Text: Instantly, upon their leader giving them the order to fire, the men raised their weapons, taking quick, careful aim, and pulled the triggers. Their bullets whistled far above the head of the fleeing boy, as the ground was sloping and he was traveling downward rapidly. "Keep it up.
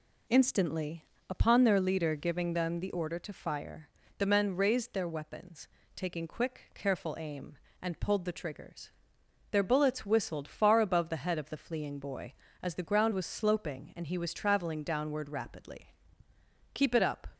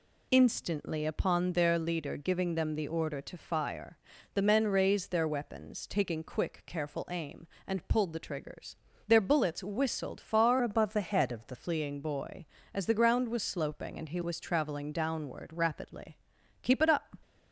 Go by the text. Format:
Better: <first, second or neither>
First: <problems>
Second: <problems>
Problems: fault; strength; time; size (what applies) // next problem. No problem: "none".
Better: first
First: none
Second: changes voice from "above" to "the"; from 10.6 to 11.5 s; 0.9 s long